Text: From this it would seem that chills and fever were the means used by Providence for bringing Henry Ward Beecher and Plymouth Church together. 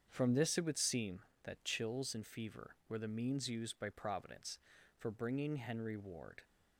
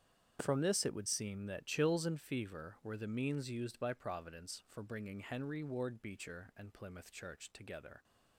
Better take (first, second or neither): second